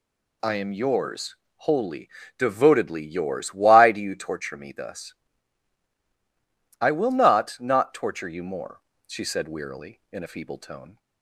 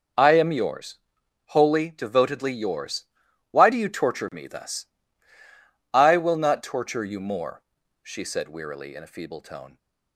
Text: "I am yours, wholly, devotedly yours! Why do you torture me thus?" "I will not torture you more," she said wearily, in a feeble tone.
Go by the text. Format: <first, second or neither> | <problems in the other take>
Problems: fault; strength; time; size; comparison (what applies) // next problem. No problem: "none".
second | says "not" twice; at 7.5 s